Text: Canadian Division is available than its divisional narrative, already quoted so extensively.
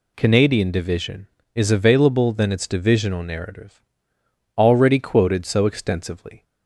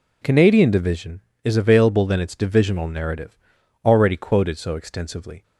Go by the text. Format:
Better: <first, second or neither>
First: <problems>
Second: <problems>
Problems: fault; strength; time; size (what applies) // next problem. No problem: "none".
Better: neither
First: none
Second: none